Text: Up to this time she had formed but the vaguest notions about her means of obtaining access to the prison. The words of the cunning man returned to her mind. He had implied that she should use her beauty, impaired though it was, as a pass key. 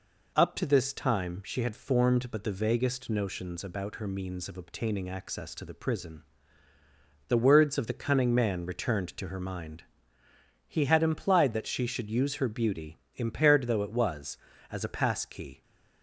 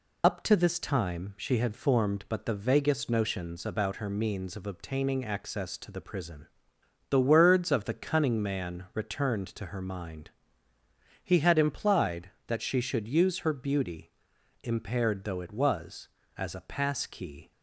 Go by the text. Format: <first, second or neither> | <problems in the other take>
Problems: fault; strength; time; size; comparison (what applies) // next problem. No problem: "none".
first | loses the start of "Up"; at 0.2 s; 60 ms